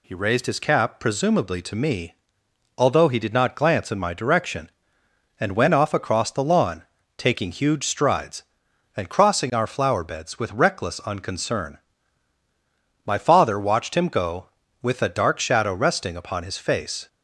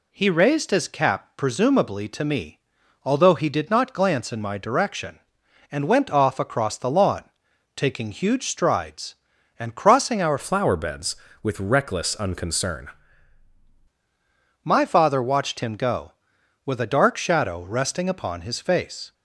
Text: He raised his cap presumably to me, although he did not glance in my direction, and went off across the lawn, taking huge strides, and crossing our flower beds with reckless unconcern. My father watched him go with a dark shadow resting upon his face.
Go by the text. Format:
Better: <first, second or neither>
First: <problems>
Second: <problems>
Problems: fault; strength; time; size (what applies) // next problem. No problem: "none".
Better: first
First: none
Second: changes voice from "flower" to "unconcern"; from 10.3 to 12.8 s; 2.5 s long